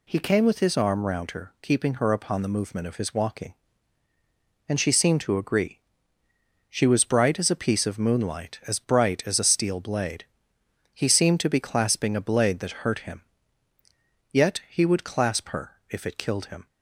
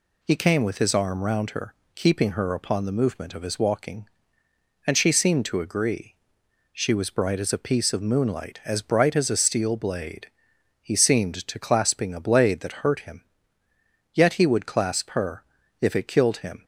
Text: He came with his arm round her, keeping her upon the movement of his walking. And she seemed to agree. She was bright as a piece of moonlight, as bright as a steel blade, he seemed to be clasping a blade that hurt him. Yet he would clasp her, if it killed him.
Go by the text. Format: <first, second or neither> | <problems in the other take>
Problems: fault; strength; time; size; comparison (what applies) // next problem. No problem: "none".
first | skips "be"; at 11.6 s